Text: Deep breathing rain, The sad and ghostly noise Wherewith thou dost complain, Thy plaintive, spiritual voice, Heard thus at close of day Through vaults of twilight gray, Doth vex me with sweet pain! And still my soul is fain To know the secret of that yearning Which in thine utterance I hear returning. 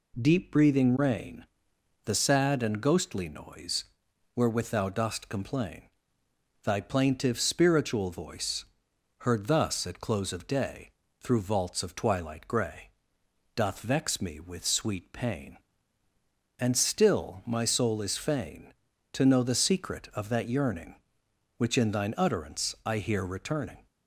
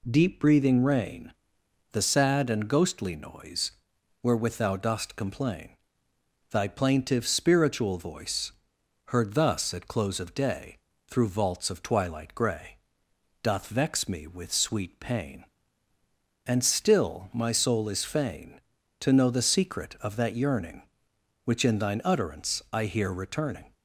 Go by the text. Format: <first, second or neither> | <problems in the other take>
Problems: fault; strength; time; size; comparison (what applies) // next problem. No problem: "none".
neither | pauses between "noise" and "Wherewith"; noticeable; the same in both // pauses between "day" and "Through"; slight; the same in both